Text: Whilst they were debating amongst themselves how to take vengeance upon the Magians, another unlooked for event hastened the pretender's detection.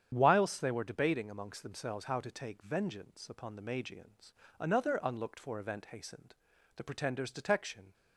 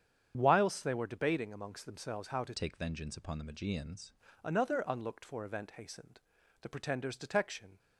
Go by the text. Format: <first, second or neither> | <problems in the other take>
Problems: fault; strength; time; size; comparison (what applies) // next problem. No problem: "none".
first | starts louder than the rest; strong; until 1.3 s; 8.5 dB; strong in the first // changes voice from "take" to "Magians"; from 2.5 to 4.1 s; 1.6 s long // pauses between "hastened" and "the"; at 6.2 s; 0.40 s long; also in the first